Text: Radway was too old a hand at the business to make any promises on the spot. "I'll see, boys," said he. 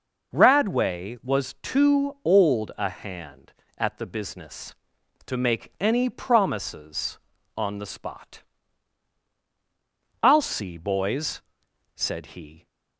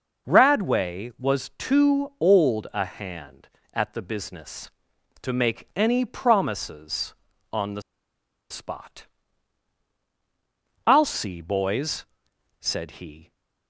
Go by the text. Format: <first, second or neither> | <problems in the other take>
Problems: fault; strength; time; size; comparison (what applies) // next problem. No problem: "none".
first | pauses between "the" and "spot"; noticeable; at 7.8 s; 0.68 s long